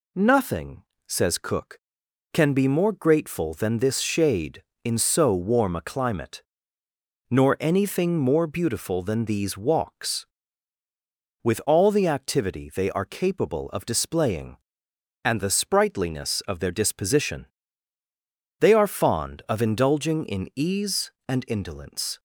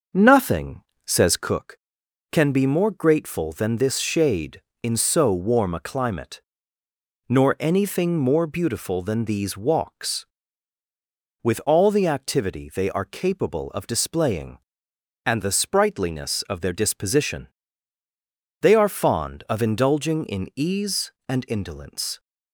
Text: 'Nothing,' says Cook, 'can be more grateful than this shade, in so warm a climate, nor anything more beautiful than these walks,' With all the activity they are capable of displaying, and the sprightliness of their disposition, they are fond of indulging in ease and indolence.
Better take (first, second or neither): first